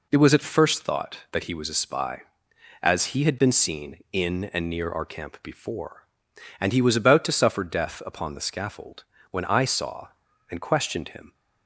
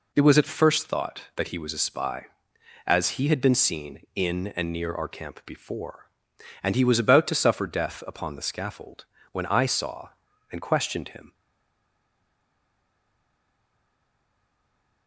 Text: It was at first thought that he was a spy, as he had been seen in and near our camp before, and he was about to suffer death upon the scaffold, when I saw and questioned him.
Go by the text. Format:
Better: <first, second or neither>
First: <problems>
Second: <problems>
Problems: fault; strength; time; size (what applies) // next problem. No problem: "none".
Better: first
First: none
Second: stays silent after the last word; strong; from 11.3 s on; 3.7 s long